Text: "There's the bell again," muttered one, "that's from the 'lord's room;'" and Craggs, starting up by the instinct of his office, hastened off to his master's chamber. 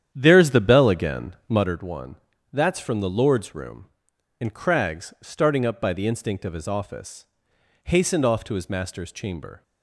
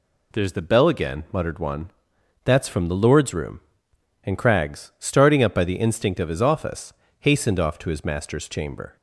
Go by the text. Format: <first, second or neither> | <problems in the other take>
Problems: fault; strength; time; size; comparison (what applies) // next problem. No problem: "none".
second | starts louder than the rest; strong; until 1.8 s; 9.5 dB